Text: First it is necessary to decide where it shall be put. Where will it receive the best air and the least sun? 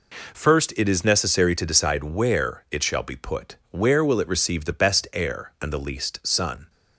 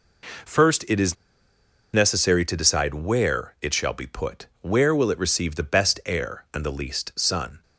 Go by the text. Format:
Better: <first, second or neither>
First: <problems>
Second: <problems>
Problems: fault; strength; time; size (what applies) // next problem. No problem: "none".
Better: first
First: none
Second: pauses between "is" and "necessary"; noticeable; at 1.1 s; 0.78 s long